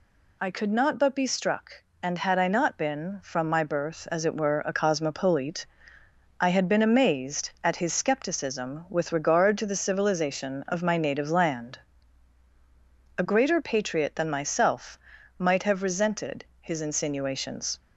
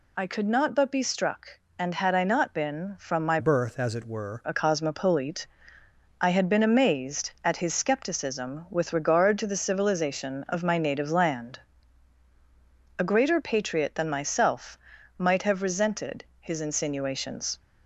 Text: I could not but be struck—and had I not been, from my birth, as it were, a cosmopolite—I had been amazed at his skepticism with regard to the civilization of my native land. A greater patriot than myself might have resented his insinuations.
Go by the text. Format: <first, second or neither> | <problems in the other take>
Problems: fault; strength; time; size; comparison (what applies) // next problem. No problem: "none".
first | changes voice from "birth" to "were"; from 3.3 to 4.4 s; 1.1 s long // pauses between "myself" and "might"; at 14.7 s; 0.40 s long; also in the first // pauses between "resented" and "his"; slight; at 16.2 s; 0.16 s long; slight in the first